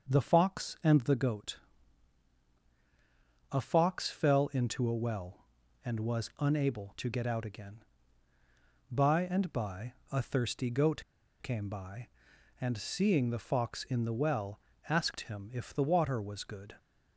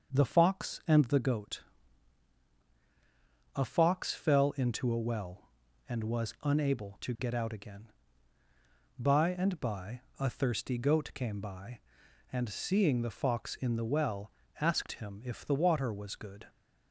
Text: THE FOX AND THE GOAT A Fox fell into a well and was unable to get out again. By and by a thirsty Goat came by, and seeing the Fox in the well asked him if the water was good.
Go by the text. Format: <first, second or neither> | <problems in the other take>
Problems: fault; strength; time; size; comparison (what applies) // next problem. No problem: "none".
second | starts louder than the rest; until 1.1 s; 6.5 dB; also in the second // pauses between "GOAT" and "A"; strong; at 1.5 s; 1.9 s long; strong in the second // pauses between "by" and "a"; slight; at 9.9 s; 0.18 s long; slight in the second // pauses between "Goat" and "came"; at 11.0 s; 0.40 s long // pauses between "well" and "asked"; slight; at 14.5 s; 0.30 s long; slight in the second